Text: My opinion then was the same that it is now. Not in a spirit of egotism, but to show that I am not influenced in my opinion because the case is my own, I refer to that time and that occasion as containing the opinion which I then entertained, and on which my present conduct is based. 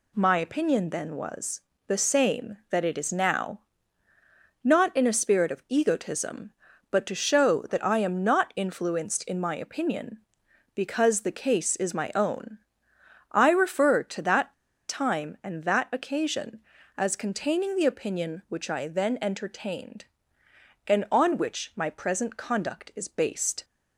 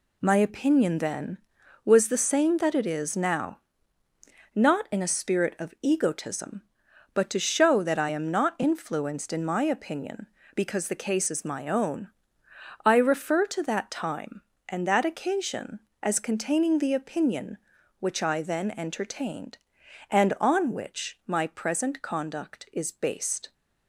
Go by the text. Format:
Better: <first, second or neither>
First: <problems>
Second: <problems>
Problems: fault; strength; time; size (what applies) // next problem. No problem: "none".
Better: second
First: pauses between "was" and "the"; slight; at 1.6 s; 0.26 s long // pauses between "that" and "time"; slight; at 14.5 s; 0.34 s long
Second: none